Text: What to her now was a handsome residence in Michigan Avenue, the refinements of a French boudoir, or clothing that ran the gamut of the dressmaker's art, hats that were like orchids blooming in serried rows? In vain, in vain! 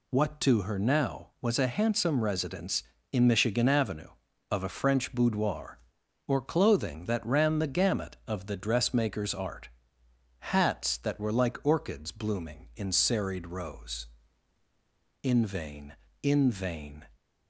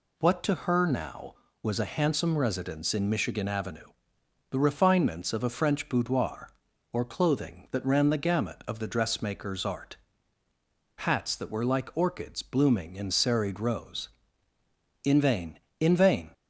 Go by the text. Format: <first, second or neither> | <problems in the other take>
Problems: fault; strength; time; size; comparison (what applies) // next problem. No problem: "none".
second | skips "the refinements"; at 4.2 s